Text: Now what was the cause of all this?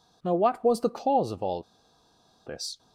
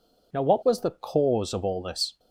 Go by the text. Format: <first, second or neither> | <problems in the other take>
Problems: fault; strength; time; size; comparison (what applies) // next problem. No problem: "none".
second | pauses between "all" and "this"; noticeable; at 1.6 s; 0.83 s long